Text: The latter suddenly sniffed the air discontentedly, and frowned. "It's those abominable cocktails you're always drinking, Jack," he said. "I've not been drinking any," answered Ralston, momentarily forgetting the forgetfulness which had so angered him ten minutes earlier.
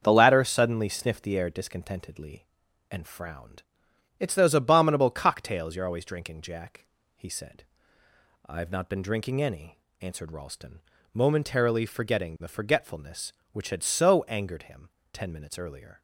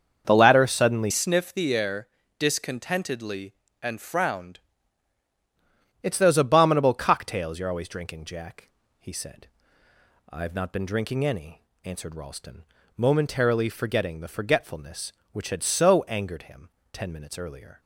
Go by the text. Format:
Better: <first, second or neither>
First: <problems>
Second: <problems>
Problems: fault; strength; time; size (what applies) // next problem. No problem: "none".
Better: first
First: starts louder than the rest; until 1.0 s; 7 dB // pauses between "him" and "ten"; slight; at 14.9 s; 0.20 s long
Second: starts louder than the rest; until 1.2 s; 6.5 dB // changes voice from "sniffed" to "frowned"; from 1.1 to 4.5 s; 3.4 s long // pauses between "air" and "discontentedly"; slight; at 2.0 s; 0.30 s long // pauses between "him" and "ten"; slight; at 16.7 s; 0.20 s long